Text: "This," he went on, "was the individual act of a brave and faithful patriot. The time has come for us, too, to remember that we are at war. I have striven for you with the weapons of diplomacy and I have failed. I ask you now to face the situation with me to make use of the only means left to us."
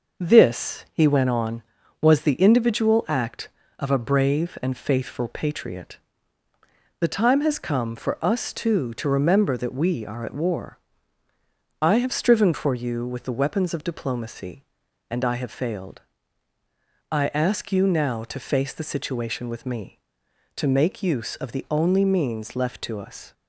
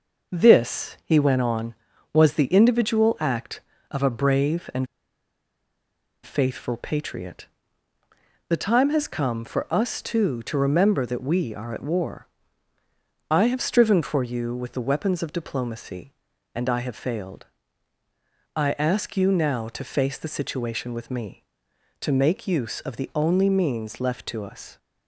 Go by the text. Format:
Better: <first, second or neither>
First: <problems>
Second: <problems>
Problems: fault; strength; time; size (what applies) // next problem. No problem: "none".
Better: first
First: none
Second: pauses between "and" and "faithful"; strong; at 4.8 s; 1.3 s long